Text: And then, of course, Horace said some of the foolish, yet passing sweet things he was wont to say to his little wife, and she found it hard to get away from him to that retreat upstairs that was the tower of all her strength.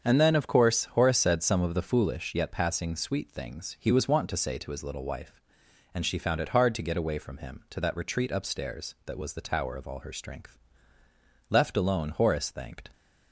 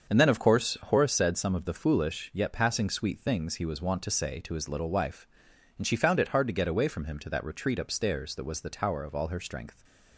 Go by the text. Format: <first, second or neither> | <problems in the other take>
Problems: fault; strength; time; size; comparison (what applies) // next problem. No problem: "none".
second | starts louder than the rest; until 1.0 s; 7 dB; also in the second // goes on to say "Left alone Horace thanked"; from 11.4 s on; 1.4 s long